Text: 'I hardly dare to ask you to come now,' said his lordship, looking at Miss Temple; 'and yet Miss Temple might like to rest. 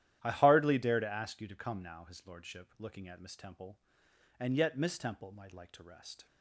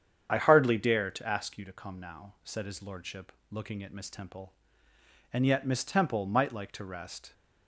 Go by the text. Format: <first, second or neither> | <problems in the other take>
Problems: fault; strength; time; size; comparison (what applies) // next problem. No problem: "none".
second | starts louder than the rest; strong; until 1.2 s; 12 dB; strong in the second // skips "said"; at 2.0 s